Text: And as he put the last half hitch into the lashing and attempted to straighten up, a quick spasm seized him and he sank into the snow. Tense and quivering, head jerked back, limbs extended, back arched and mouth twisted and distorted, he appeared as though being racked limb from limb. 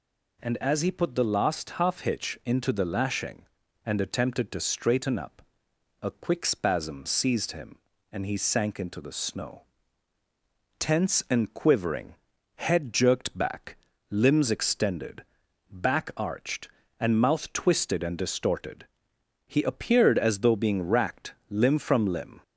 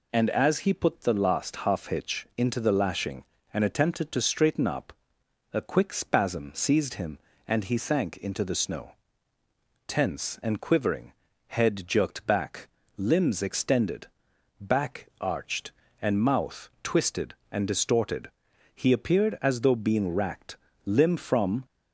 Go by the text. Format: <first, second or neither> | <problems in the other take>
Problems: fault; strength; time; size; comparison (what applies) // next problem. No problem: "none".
first | pauses between "racked" and "limb"; slight; at 20.5 s; 0.28 s long; slight in the first // stops before "limb"; at 21.6 s